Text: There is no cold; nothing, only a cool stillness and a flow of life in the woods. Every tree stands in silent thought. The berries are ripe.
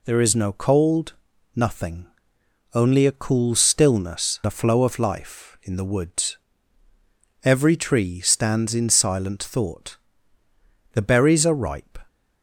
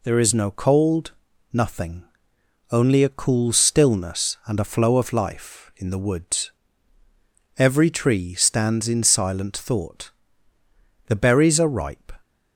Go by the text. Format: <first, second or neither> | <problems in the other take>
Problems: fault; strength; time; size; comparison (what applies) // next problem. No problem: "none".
second | skips "and"; at 4.4 s